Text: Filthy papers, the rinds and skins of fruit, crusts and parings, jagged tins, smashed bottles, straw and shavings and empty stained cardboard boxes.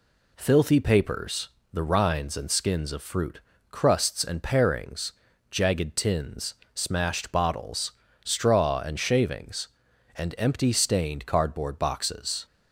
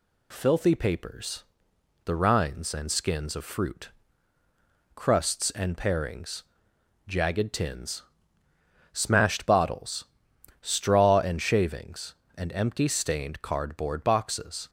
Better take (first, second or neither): neither